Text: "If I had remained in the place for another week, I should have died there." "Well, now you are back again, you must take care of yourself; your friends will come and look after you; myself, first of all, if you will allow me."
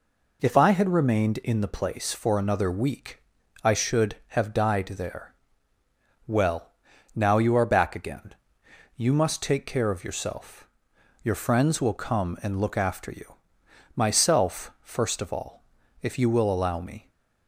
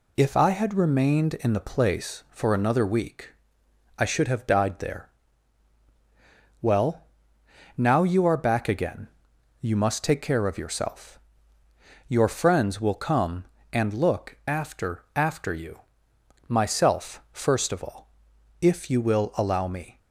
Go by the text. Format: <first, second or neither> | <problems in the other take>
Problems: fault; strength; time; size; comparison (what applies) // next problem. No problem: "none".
first | says "after" twice; at 15.1 s